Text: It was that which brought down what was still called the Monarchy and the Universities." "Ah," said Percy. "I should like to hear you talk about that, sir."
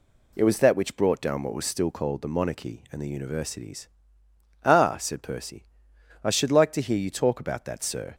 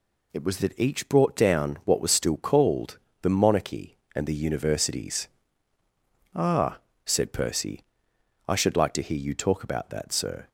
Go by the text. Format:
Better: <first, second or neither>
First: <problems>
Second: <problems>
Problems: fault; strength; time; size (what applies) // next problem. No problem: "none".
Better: first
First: none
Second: says "each" for "which"; at 0.7 s // pauses between "called" and "the"; slight; at 2.9 s; 0.24 s long